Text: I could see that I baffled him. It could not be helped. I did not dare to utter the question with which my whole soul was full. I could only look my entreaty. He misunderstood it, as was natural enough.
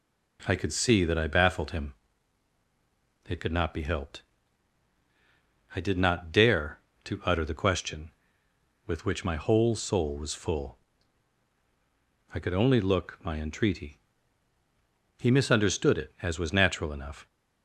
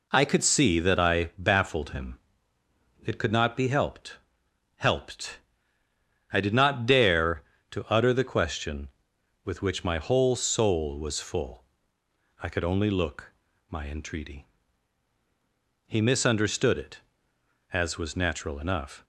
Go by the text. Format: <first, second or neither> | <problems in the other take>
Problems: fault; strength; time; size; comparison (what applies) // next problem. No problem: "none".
first | says "helped" twice; at 4.7 s // pauses between "look" and "my"; at 13.3 s; 0.38 s long